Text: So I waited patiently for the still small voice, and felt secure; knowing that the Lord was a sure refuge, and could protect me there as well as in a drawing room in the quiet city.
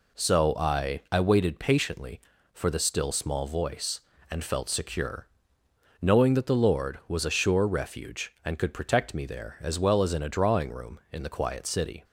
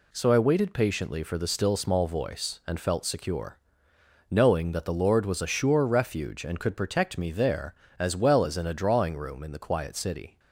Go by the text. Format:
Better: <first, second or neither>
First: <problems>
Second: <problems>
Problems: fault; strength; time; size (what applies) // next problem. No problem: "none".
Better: second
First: says "I" twice; at 1.1 s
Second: none